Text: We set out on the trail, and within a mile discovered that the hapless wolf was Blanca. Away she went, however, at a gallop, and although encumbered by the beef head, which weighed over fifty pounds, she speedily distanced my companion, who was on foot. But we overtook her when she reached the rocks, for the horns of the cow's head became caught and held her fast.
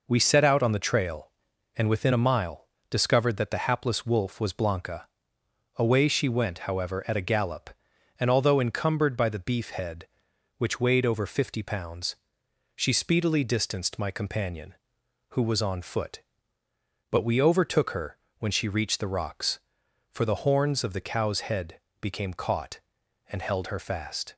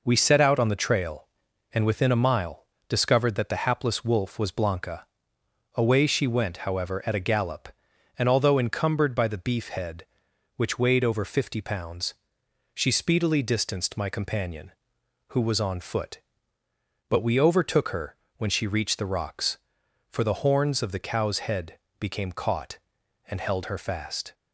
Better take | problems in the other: neither | pauses between "mile" and "discovered"; slight; the same in both // pauses between "her" and "when"; slight; the same in both // pauses between "head" and "became"; slight; the same in both

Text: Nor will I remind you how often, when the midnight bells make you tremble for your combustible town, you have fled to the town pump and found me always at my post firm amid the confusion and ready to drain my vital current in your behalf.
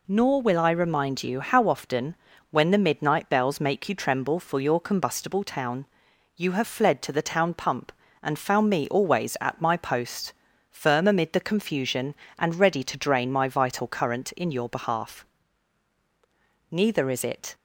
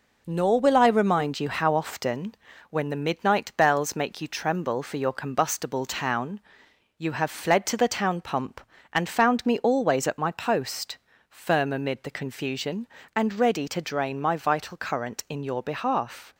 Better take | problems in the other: second | pauses between "post" and "firm"; at 10.3 s; 0.38 s long; slight in the second // goes on to say "Neither is it"; noticeable; from 16.6 s on; 0.86 s long

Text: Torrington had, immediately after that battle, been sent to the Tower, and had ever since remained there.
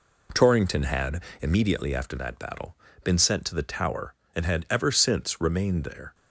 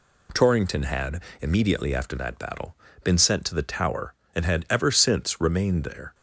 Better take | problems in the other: second | starts louder than the rest; until 1.7 s; 3.5 dB

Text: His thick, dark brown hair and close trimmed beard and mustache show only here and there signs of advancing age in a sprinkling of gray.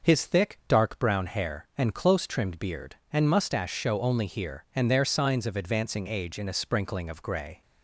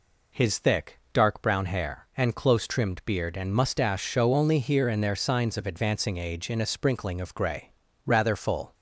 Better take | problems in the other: first | goes on to say "Rather full"; noticeable; from 8.0 s on; 0.70 s long

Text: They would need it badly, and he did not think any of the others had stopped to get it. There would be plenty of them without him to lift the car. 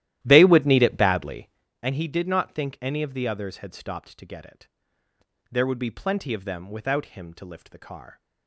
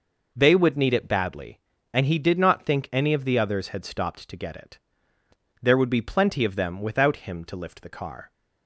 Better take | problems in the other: second | starts louder than the rest; strong; until 1.6 s; 13.5 dB

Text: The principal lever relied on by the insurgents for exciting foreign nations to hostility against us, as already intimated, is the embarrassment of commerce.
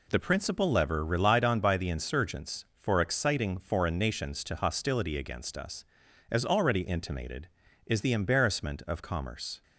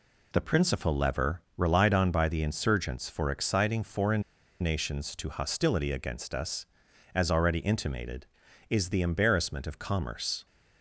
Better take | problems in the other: first | pauses between "lever" and "relied"; slight; at 1.4 s; 0.16 s long // pauses between "foreign" and "nations"; at 4.2 s; 0.38 s long

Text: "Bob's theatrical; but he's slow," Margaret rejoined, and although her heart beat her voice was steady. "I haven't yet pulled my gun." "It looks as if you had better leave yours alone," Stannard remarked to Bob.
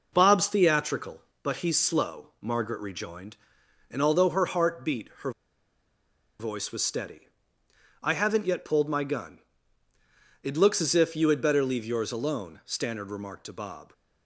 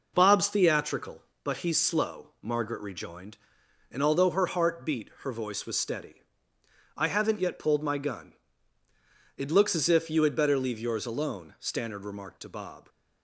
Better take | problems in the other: second | pauses between "her" and "voice"; at 5.3 s; 1.0 s long

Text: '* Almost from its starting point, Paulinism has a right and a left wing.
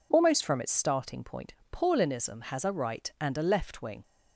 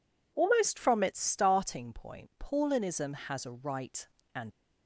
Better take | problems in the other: first | stops before "a left wing"; at 4.5 s

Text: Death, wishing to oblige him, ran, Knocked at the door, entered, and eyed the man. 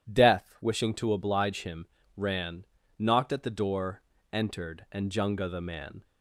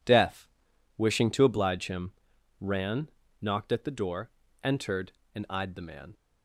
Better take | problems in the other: second | says "junga" for "eyed"; at 5.0 s

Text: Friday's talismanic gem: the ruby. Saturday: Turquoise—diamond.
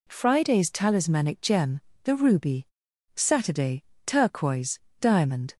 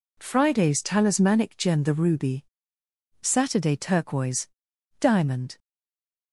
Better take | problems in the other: first | stays silent after the last word; slight; from 5.5 s on; 0.8 s long

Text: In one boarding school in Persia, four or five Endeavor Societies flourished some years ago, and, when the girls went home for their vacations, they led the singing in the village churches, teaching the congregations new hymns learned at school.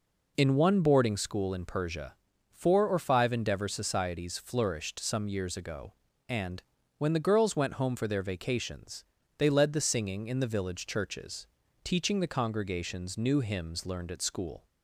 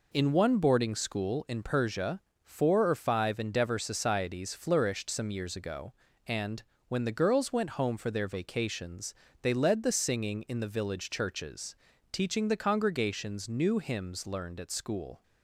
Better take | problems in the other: neither | none

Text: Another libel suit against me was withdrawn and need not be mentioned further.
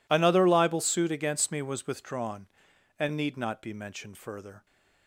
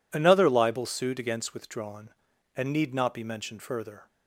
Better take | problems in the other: first | skips "me was"; at 1.5 s

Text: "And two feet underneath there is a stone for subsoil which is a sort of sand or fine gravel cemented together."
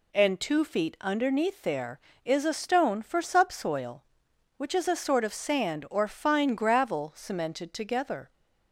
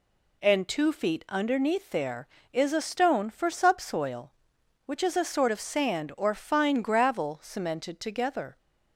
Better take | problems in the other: neither | none

